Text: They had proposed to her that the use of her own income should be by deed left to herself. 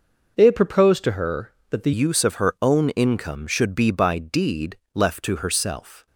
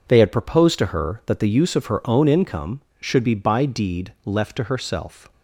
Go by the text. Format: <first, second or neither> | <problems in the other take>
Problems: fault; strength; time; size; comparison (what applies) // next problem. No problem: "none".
second | changes voice at "use"; from 1.9 s on; 4.1 s long // pauses between "deed" and "left"; slight; at 4.7 s; 0.18 s long